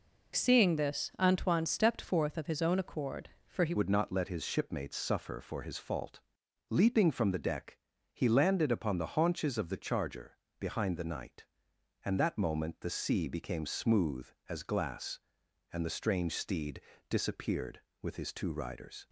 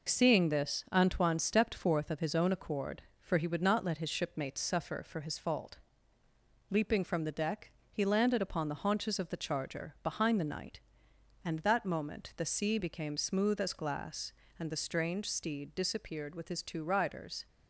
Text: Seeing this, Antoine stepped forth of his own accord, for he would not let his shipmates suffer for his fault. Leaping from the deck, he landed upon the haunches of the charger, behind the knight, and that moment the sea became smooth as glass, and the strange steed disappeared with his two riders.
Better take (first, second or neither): second